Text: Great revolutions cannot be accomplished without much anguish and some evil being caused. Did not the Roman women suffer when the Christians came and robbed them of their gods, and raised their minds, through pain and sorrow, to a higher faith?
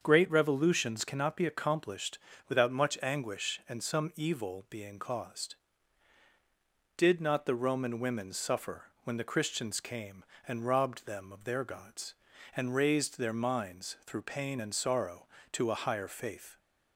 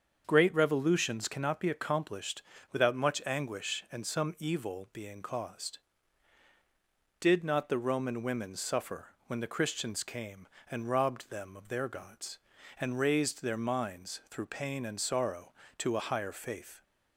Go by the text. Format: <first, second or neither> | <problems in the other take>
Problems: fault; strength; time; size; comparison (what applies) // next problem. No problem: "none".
neither | starts louder than the rest; the same in both // pauses between "accomplished" and "without"; slight; the same in both // pauses between "suffer" and "when"; slight; the same in both